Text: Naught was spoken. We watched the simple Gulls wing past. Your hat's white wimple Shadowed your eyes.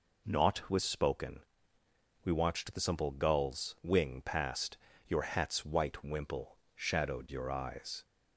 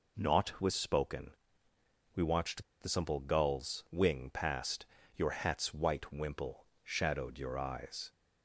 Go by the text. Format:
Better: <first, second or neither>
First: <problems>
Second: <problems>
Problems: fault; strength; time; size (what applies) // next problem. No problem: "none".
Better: first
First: pauses between "wimple" and "Shadowed"; slight; at 6.5 s; 0.20 s long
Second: pauses between "watched" and "the"; slight; at 2.6 s; 0.18 s long // pauses between "wimple" and "Shadowed"; slight; at 6.6 s; 0.20 s long